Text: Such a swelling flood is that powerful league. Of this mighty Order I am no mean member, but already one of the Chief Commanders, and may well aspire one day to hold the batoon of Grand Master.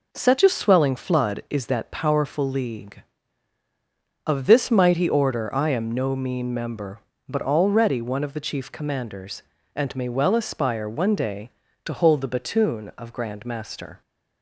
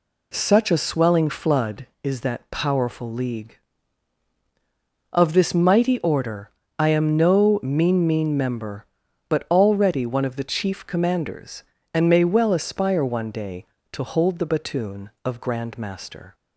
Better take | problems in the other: first | pauses between "Order" and "I"; slight; at 6.4 s; 0.30 s long // says "mean" twice; at 8.0 s

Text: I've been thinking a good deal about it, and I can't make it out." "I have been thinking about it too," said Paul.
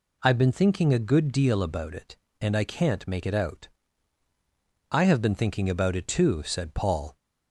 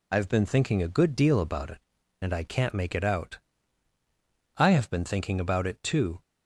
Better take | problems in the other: first | stops before "said Paul"; at 6.2 s

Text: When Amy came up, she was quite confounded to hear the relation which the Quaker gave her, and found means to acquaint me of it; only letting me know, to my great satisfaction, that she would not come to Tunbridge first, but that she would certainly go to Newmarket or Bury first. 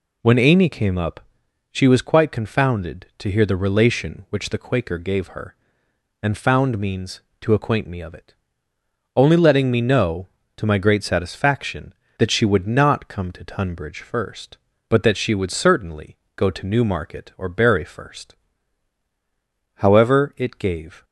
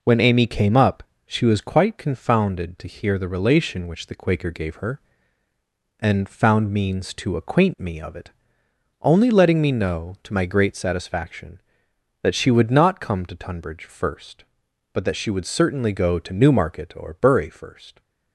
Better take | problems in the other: second | pauses between "certainly" and "go"; slight; at 16.1 s; 0.18 s long // goes on to say "However it gave"; noticeable; from 19.7 s on; 1.2 s long

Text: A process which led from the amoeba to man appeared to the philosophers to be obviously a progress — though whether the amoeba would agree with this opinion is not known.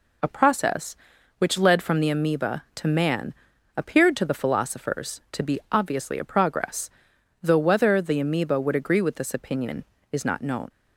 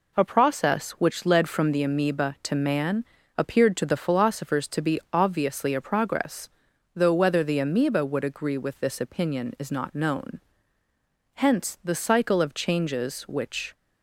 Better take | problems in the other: first | pauses between "man" and "appeared"; slight; at 3.0 s; 0.32 s long; also in the first // goes on to say "Hence the cycle of changes which"; strong; from 11.3 s on; 2.3 s long

